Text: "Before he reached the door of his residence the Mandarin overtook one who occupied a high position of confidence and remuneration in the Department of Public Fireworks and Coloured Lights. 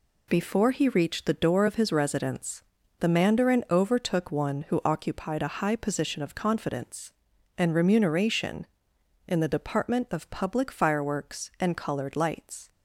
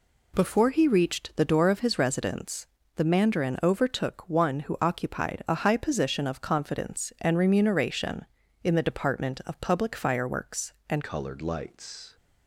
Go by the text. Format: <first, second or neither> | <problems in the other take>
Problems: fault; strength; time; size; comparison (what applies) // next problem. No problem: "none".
first | pauses between "residence" and "the"; slight; at 2.6 s; 0.30 s long; also in the first // changes voice at "Coloured"; from 11.0 s on; 1.1 s long